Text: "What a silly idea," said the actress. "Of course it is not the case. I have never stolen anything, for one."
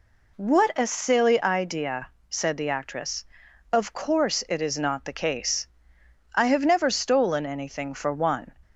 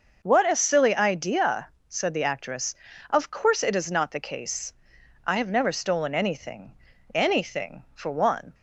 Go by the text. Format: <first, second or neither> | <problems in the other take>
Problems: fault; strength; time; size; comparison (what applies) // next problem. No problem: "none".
first | says "anything" twice; at 7.1 s